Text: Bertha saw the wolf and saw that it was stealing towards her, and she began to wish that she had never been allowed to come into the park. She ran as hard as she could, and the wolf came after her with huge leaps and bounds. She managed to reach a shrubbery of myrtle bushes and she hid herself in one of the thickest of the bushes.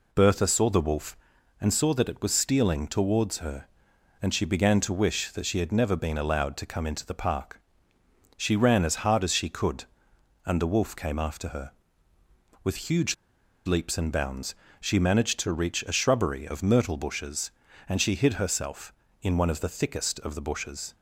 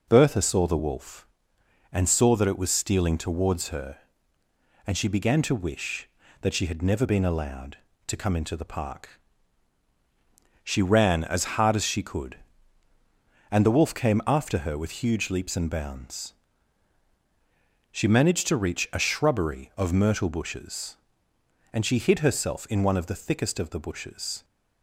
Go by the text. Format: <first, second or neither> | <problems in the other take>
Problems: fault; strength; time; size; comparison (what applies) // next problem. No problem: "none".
second | pauses between "huge" and "leaps"; noticeable; at 13.1 s; 0.51 s long